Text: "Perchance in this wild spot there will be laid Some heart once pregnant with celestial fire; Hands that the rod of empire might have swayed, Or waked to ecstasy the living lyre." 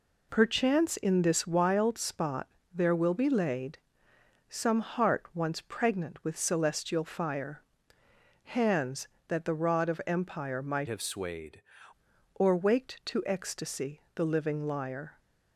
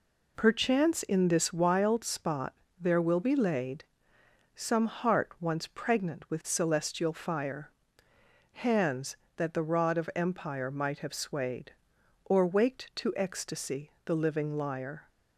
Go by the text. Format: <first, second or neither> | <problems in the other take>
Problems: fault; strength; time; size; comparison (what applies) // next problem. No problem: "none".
second | pauses between "spot" and "there"; slight; at 2.4 s; 0.24 s long; slight in the second // pauses between "laid" and "Some"; noticeable; at 3.7 s; 0.70 s long; noticeable in the second // changes voice from "have" to "swayed"; from 10.8 to 11.6 s; 0.8 s long